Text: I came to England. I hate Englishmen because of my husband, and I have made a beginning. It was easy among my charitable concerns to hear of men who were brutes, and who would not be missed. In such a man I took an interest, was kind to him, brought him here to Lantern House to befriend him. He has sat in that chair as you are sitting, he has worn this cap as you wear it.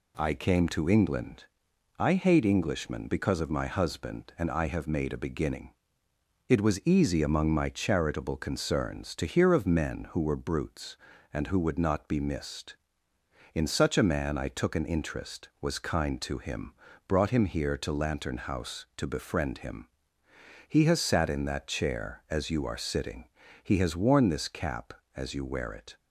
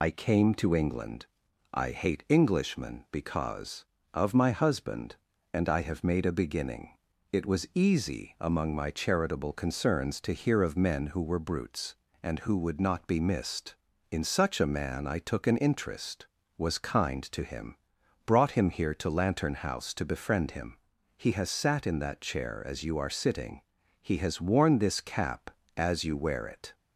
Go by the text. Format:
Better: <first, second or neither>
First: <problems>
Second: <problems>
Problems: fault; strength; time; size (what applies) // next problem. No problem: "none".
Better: first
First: none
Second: loses the start of "I"; at 0.0 s; 50 ms